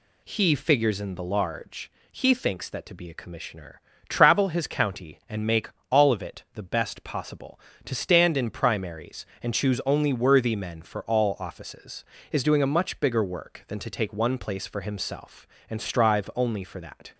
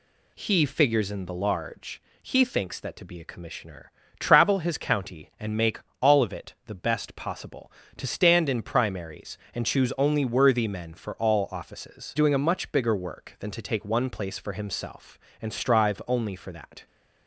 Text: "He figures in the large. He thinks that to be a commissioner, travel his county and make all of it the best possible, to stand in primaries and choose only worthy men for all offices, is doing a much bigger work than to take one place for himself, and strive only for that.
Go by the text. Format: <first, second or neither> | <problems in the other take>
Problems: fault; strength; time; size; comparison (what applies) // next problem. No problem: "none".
first | pauses between "make" and "all"; slight; at 5.7 s; 0.20 s long; slight in the first // skips "is"; at 12.1 s